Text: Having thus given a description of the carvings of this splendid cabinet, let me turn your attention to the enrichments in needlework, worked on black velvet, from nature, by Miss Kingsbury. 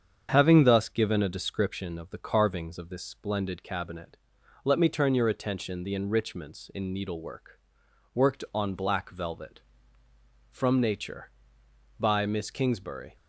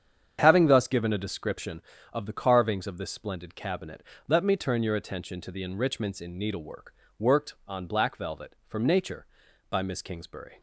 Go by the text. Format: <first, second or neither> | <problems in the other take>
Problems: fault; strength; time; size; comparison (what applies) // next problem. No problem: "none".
second | starts louder than the rest; strong; until 1.3 s; 7.5 dB; strong in the second // skips "to"; at 5.8 s